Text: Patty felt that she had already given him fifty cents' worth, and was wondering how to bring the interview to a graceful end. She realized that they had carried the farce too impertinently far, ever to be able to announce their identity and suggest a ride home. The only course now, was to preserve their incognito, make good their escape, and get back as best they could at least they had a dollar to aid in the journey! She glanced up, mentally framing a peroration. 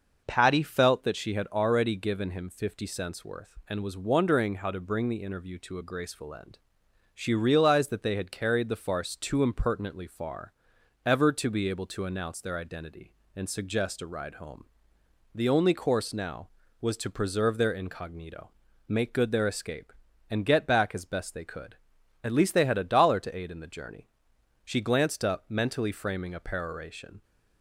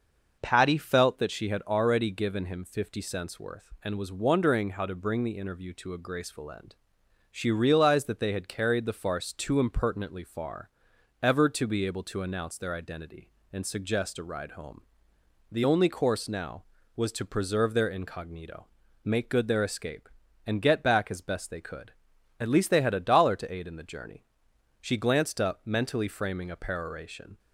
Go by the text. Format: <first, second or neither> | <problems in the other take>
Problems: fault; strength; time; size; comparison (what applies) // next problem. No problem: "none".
neither | starts louder than the rest; noticeable; the same in both